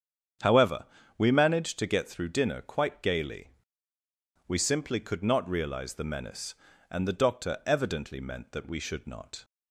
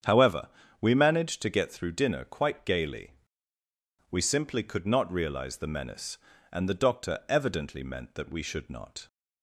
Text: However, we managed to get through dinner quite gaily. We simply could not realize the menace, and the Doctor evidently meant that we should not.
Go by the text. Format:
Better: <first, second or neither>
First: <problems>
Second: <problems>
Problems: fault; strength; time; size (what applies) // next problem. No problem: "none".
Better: neither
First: starts louder than the rest; strong; until 1.7 s; 8.5 dB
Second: starts louder than the rest; strong; until 1.3 s; 8.5 dB